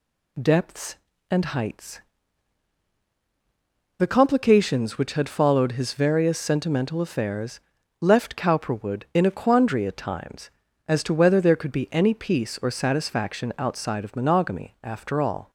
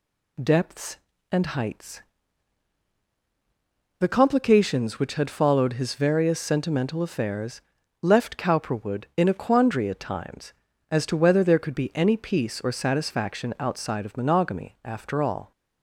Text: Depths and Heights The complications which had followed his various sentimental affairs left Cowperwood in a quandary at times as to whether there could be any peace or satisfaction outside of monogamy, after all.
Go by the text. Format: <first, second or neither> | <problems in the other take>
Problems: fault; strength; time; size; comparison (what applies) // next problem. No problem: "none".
neither | pauses between "Heights" and "The"; strong; the same in both // pauses between "affairs" and "left"; the same in both